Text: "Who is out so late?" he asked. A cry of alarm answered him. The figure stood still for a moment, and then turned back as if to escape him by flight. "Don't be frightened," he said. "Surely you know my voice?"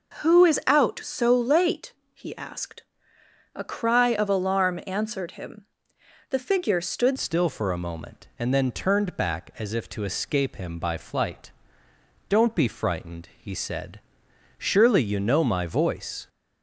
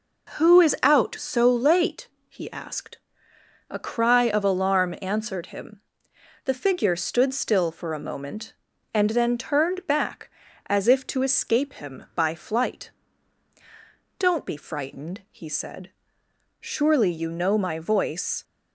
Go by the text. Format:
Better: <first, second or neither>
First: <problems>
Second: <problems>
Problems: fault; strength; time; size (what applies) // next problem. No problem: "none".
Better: second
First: changes voice at "still"; from 7.1 s on; 9.1 s long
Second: none